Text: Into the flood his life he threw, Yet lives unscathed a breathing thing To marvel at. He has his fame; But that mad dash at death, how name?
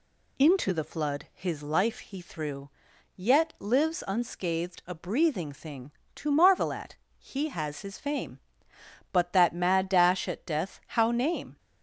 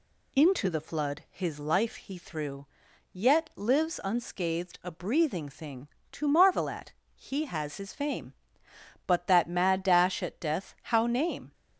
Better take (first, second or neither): neither